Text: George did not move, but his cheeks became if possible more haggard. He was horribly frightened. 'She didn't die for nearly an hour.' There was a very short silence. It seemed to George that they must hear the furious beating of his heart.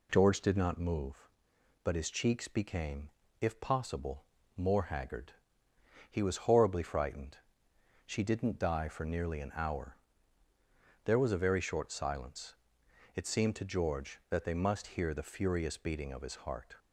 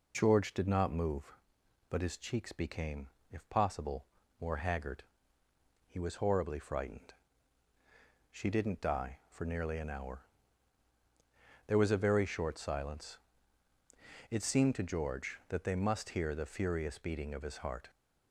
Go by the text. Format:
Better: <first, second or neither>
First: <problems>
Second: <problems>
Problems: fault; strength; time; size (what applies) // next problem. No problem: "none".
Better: neither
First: pauses between "became" and "if"; slight; at 3.1 s; 0.30 s long // pauses between "possible" and "more"; slight; at 4.2 s; 0.32 s long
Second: pauses between "became" and "if"; slight; at 3.0 s; 0.22 s long // pauses between "possible" and "more"; slight; at 4.0 s; 0.34 s long